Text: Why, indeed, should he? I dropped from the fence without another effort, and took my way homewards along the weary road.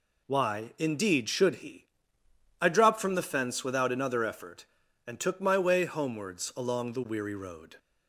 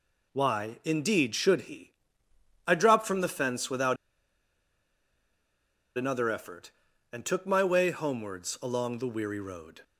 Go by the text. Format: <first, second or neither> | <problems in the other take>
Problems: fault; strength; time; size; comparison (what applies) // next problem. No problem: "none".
first | pauses between "without" and "another"; strong; at 3.9 s; 2.0 s long